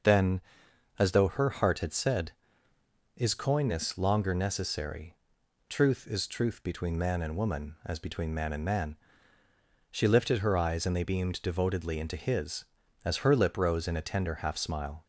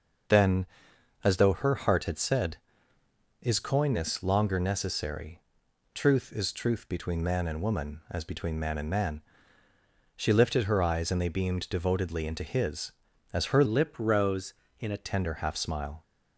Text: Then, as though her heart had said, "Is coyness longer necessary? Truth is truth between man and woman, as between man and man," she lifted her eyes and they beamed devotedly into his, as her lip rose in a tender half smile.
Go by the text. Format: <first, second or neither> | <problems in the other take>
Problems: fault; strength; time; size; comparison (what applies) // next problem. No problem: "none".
first | changes voice from "lip" to "a"; from 13.6 to 15.0 s; 1.4 s long